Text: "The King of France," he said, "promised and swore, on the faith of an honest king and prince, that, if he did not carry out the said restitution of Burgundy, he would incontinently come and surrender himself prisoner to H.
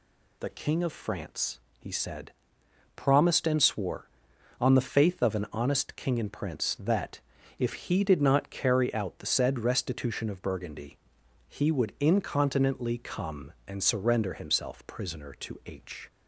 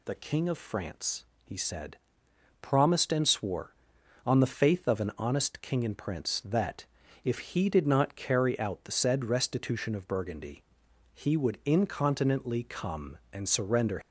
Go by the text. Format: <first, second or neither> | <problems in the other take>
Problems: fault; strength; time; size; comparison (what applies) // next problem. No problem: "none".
first | stops before "himself prisoner to H"; at 14.0 s